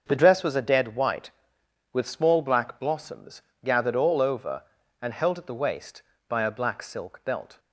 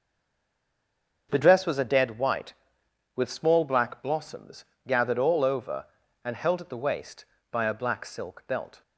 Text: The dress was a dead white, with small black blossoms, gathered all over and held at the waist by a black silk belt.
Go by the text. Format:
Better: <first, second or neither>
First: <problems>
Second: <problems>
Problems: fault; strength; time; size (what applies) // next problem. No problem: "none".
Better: first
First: starts louder than the rest; until 1.0 s; 6.5 dB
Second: stays silent before the first word; noticeable; until 1.2 s; 1.2 s long // starts louder than the rest; until 2.3 s; 6.5 dB